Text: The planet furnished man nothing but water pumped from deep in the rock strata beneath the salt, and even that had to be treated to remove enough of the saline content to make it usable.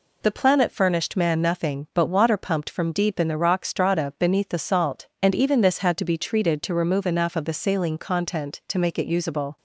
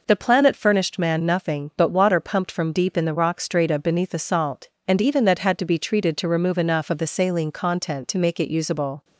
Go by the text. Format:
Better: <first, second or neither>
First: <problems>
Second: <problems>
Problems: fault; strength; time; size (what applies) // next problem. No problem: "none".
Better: second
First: says "this" for "that"; at 5.6 s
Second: none